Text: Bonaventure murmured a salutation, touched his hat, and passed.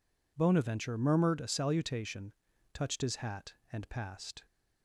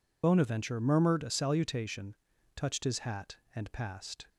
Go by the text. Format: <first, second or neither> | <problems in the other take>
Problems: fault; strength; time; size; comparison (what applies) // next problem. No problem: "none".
first | loses the start of "Bonaventure"; at 0.2 s; 60 ms